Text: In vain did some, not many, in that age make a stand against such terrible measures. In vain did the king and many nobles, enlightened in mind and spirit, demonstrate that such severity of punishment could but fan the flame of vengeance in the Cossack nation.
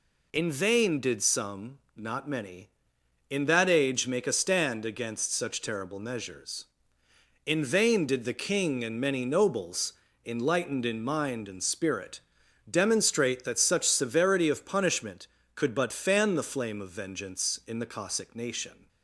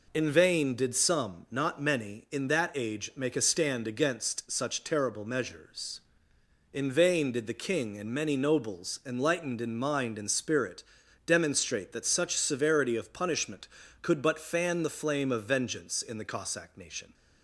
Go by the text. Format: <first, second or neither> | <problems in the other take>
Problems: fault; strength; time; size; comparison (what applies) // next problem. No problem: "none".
neither | none